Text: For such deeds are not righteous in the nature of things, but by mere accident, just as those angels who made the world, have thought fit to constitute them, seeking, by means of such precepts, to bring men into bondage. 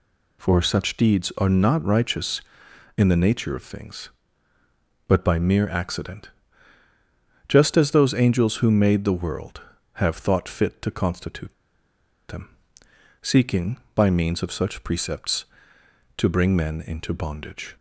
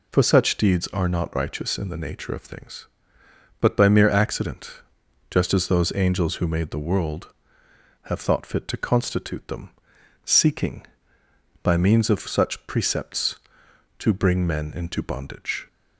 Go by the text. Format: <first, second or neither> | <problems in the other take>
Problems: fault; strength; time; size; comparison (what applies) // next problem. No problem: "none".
second | pauses between "constitute" and "them"; noticeable; at 11.5 s; 0.76 s long